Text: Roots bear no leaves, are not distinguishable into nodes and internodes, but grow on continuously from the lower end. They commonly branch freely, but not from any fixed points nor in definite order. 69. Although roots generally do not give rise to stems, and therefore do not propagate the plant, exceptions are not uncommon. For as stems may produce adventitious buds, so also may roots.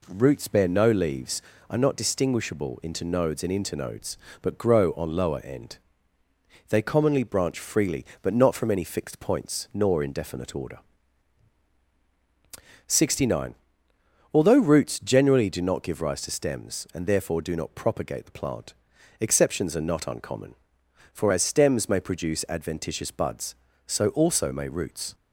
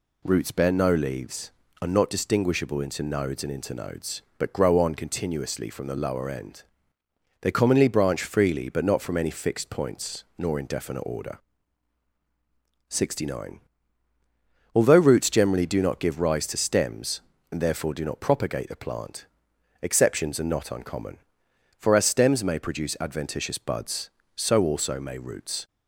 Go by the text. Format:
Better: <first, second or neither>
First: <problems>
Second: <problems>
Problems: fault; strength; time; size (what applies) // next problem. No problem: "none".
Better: second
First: skips "continuously from the"; at 5.1 s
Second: none